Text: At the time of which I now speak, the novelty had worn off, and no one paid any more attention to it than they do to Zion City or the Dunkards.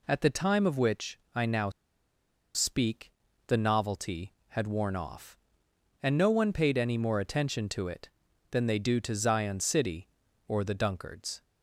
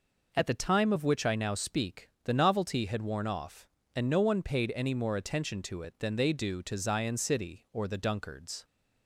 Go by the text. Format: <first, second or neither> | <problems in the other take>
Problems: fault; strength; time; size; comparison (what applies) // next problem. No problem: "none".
second | pauses between "which" and "I"; slight; at 1.1 s; 0.16 s long // pauses between "now" and "speak"; noticeable; at 1.6 s; 0.85 s long